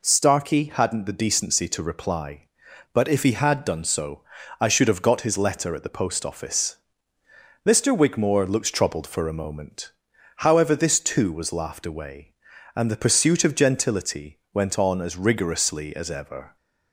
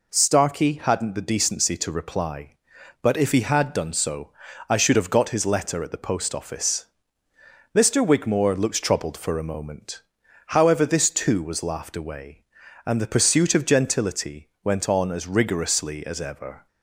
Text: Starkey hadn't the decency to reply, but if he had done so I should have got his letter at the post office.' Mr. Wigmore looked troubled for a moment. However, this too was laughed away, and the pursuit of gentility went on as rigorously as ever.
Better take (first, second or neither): neither